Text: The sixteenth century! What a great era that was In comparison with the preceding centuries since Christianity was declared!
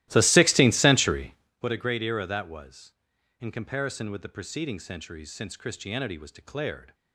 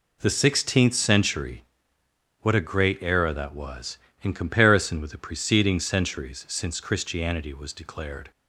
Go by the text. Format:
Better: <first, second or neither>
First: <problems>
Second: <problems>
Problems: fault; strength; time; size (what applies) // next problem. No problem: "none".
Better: second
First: starts louder than the rest; strong; until 1.6 s; 16 dB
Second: none